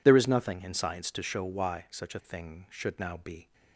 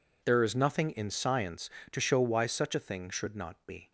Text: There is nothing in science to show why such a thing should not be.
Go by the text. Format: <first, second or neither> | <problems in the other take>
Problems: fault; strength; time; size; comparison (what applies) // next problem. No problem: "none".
second | says "now" for "not"; at 2.9 s